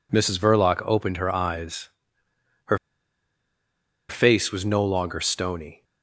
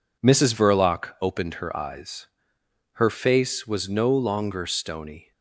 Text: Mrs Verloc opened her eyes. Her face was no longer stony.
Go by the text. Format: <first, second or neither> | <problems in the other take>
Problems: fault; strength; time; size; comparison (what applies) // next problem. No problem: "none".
second | pauses between "Her" and "face"; strong; at 2.7 s; 1.3 s long